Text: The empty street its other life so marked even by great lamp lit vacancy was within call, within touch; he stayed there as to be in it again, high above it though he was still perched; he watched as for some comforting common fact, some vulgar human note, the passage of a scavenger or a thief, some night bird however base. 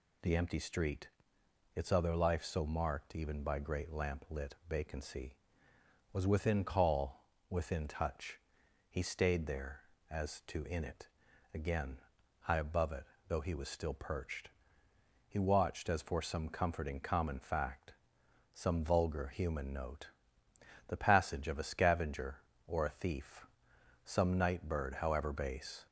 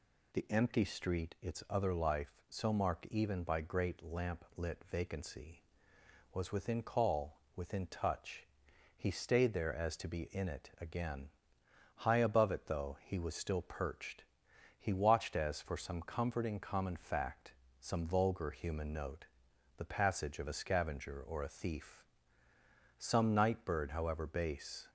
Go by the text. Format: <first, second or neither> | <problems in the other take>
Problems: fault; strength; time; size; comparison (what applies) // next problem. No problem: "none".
second | pauses between "street" and "its"; noticeable; at 1.0 s; 0.66 s long // skips "be"; at 10.6 s // pauses between "it" and "again"; noticeable; at 11.0 s; 0.46 s long // pauses between "it" and "though"; slight; at 13.0 s; 0.24 s long